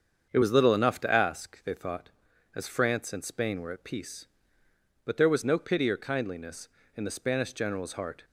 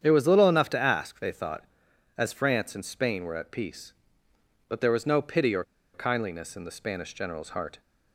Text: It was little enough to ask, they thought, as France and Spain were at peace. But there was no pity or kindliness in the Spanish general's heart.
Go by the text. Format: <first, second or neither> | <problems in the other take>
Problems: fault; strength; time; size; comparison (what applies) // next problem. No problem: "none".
first | starts louder than the rest; strong; until 1.0 s; 8.5 dB; strong in the first // pauses between "or" and "kindliness"; slight; at 5.6 s; 0.30 s long